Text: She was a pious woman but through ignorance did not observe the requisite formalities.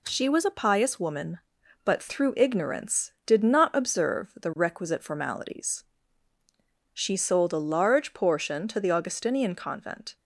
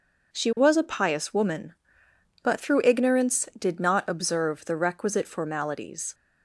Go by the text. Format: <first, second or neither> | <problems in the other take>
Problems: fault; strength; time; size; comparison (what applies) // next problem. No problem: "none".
second | goes on to say "She sold a large portion to the Augustinian convent"; strong; from 6.9 s on; 3.2 s long